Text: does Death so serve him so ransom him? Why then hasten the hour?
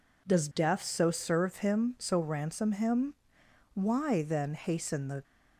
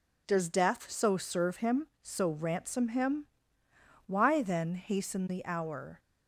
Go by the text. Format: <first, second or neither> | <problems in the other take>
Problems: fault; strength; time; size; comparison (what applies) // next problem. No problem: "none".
second | stops before "hour"; at 5.2 s